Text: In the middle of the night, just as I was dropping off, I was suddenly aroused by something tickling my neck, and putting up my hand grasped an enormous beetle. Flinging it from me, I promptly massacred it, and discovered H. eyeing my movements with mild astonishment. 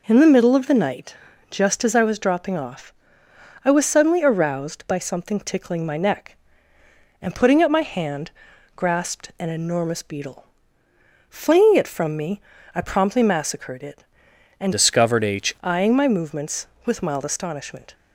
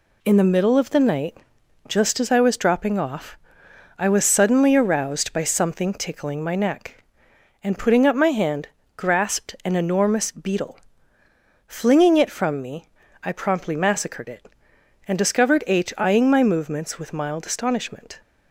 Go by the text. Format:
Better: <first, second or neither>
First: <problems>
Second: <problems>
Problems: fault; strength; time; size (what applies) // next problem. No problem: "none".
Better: second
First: pauses between "hand" and "grasped"; at 8.3 s; 0.42 s long // changes voice from "discovered" to "H"; from 14.7 to 15.5 s; 0.8 s long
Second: pauses between "hand" and "grasped"; slight; at 8.6 s; 0.30 s long